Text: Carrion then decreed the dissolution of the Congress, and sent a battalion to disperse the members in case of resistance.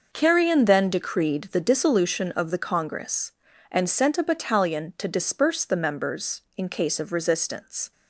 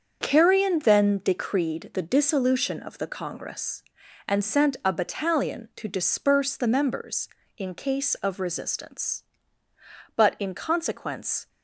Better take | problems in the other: first | starts louder than the rest; until 1.2 s; 7 dB // goes on to say "But in consequence"; from 10.1 s on; 1.3 s long

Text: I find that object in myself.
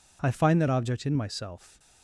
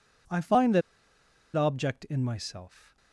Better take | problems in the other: first | pauses between "that" and "object"; noticeable; at 0.8 s; 0.74 s long

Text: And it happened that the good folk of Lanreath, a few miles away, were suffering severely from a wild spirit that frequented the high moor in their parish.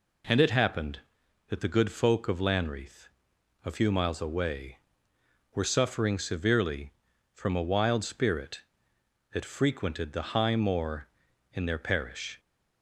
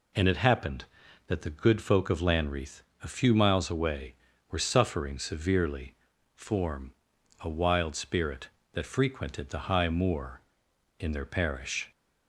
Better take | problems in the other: first | says "form" for "from"; at 6.3 s

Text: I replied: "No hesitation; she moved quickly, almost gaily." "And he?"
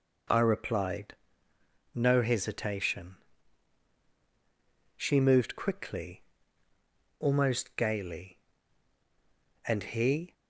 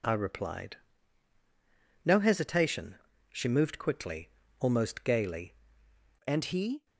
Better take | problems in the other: first | changes voice at "And"; from 6.2 s on; 0.6 s long

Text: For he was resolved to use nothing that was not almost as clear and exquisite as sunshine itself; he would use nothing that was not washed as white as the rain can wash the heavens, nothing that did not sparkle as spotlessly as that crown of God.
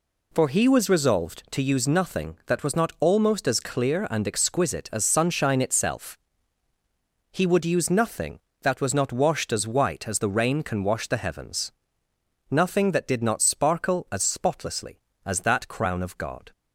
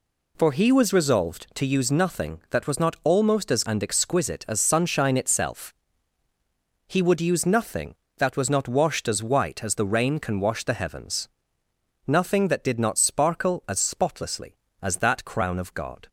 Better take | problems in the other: first | skips "clear"; at 3.6 s

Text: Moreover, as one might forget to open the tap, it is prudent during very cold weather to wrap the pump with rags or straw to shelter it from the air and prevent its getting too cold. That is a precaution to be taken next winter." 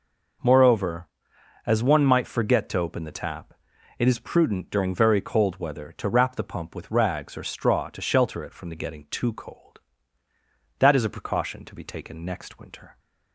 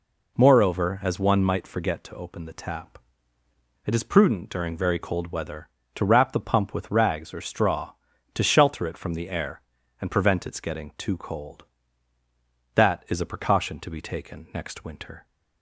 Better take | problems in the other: second | skips "air and prevent its"; at 8.7 s

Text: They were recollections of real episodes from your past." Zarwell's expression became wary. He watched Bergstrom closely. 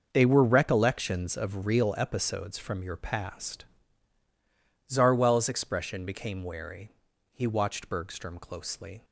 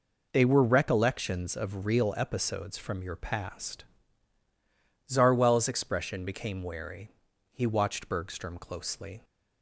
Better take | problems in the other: second | gets quieter; strong; throughout; 11.5 dB

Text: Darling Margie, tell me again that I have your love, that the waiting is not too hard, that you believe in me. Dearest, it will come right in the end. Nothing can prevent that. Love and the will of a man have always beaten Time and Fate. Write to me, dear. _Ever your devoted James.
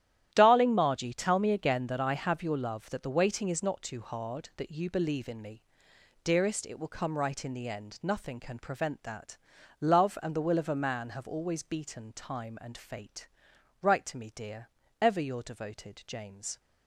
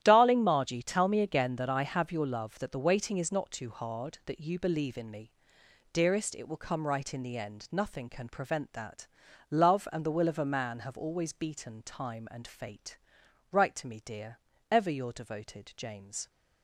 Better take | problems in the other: neither | starts louder than the rest; strong; the same in both

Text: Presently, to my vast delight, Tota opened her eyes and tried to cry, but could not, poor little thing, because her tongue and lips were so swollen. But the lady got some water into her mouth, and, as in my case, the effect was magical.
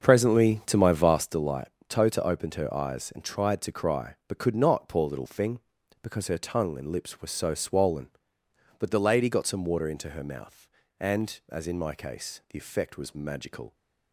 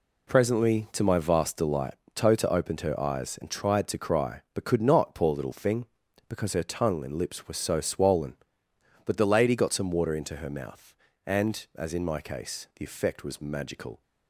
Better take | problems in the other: second | starts louder than the rest; until 1.4 s; 6.5 dB

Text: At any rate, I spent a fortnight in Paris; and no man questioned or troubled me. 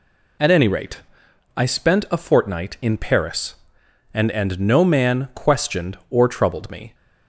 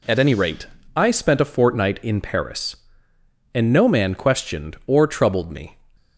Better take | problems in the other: second | says "and" twice; at 4.3 s

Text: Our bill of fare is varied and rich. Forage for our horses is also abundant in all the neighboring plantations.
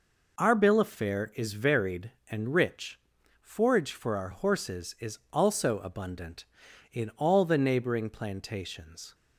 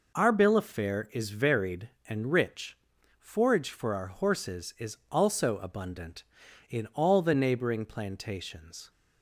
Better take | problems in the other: neither | none

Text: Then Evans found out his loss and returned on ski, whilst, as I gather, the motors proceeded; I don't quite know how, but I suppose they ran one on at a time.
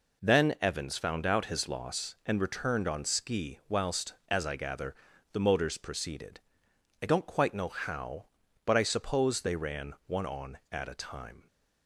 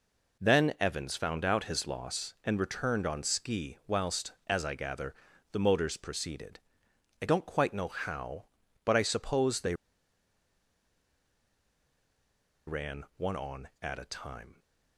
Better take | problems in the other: first | pauses between "they" and "ran"; strong; at 9.7 s; 2.9 s long

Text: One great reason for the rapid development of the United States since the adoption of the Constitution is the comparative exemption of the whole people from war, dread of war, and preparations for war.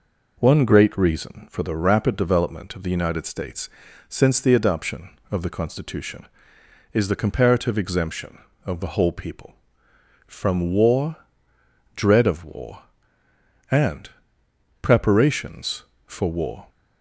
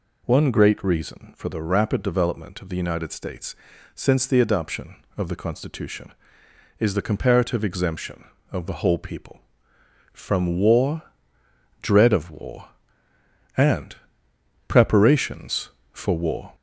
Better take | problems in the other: first | gets louder; slight; throughout; 2.5 dB // pauses between "States" and "since"; at 3.5 s; 0.38 s long; also in the first // pauses between "and" and "preparations"; noticeable; at 13.9 s; 0.70 s long; noticeable in the first

